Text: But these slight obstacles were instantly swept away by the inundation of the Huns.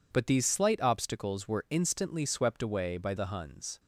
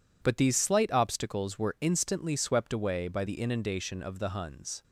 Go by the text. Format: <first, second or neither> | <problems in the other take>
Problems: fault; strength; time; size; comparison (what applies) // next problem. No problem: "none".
second | skips "the inundation of"; at 3.1 s